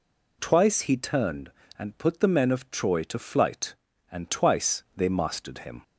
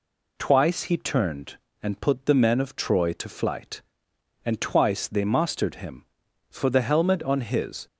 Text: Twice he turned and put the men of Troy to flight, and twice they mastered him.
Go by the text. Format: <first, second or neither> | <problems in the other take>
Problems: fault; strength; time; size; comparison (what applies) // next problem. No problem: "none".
first | goes on to say "For the helmet on his"; from 6.5 s on; 1.3 s long